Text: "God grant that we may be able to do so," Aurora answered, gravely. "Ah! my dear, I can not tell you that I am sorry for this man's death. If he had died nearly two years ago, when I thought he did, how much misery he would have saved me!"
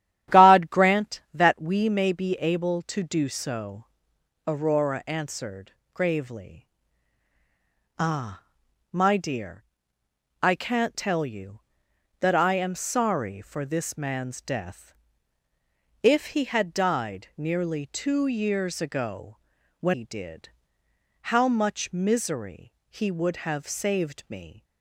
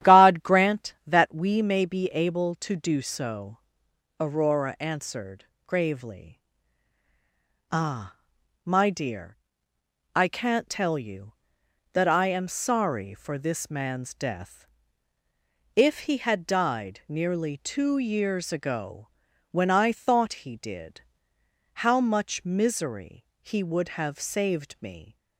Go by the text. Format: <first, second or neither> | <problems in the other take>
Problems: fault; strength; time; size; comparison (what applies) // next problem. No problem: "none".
second | starts louder than the rest; strong; until 1.4 s; 11.5 dB; strong in the second // skips "I thought"; at 19.9 s // pauses between "misery" and "he"; slight; at 22.7 s; 0.16 s long; slight in the second